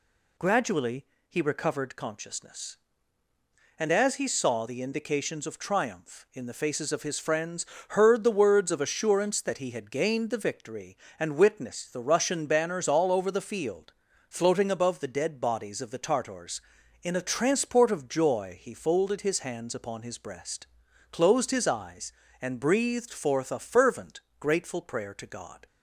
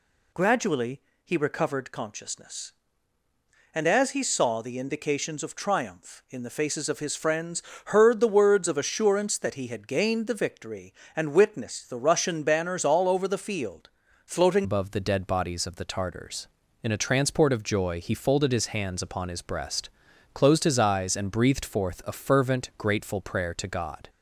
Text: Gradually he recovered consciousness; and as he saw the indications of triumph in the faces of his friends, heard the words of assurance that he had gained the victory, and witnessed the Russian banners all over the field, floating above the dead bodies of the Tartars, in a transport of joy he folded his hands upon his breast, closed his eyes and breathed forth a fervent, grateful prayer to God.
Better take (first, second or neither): first